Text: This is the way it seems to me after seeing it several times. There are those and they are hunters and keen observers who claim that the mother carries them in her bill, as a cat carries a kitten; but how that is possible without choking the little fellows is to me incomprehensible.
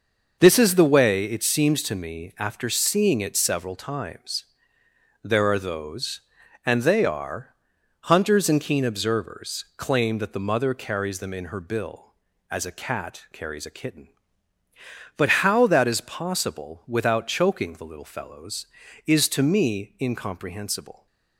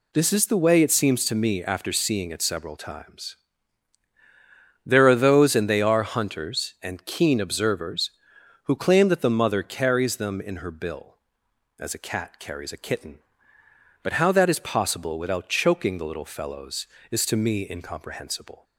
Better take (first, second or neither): second